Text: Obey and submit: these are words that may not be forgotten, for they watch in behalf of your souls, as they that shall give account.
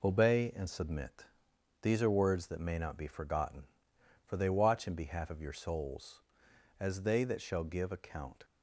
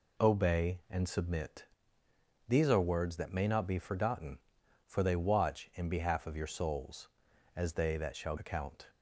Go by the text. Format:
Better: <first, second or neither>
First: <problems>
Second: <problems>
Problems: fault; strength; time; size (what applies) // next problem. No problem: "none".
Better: first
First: none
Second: skips "give"; at 8.3 s